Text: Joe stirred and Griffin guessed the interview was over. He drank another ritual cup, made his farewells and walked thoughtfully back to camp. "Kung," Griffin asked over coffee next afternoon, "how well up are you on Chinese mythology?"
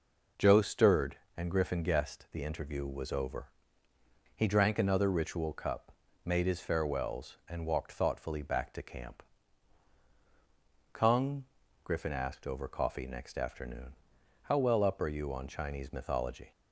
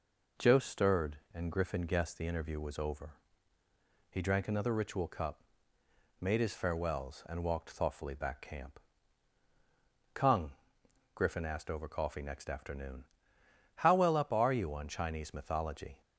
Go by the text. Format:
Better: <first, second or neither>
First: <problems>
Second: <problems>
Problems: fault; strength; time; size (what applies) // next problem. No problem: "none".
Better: first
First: none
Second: skips "to"; at 8.4 s